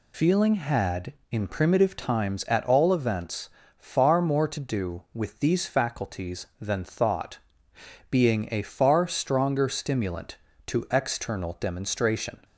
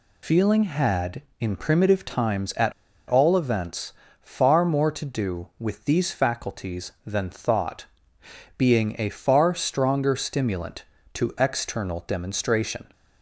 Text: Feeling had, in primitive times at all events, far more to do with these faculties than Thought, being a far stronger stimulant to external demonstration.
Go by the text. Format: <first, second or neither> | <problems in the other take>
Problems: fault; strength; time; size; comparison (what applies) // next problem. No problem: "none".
first | pauses between "at" and "all"; slight; at 2.7 s; 0.35 s long